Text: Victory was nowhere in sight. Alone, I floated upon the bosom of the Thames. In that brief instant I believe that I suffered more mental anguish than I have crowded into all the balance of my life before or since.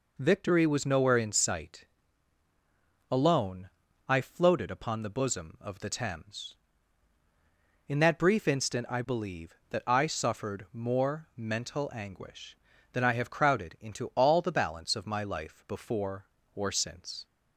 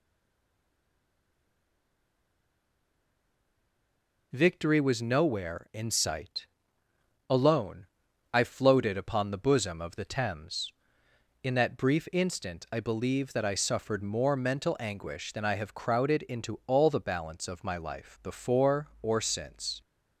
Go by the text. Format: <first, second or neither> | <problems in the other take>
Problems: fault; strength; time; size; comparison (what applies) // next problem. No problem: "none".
first | stays silent before the first word; strong; until 4.3 s; 4.3 s long